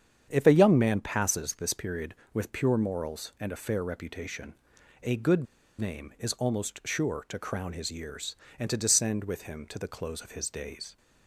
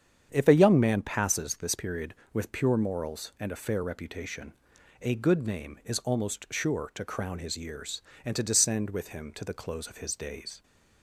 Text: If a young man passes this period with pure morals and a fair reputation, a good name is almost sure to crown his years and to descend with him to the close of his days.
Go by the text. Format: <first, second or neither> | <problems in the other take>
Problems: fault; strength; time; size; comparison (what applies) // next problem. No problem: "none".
second | starts louder than the rest; strong; until 1.3 s; 8 dB; strong in the second // pauses between "good" and "name"; slight; at 5.4 s; 0.34 s long